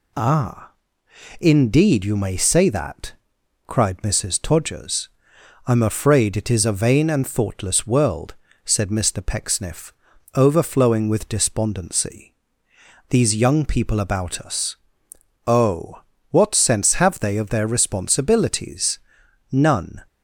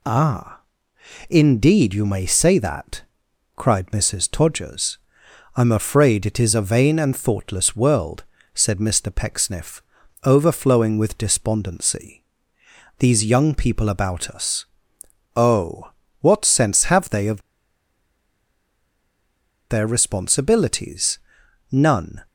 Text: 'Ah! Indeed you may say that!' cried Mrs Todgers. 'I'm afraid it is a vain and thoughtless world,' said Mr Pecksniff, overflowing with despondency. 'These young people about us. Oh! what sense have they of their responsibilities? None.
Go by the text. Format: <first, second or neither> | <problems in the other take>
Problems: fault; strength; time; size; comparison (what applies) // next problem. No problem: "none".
first | pauses between "of" and "their"; strong; at 17.4 s; 2.2 s long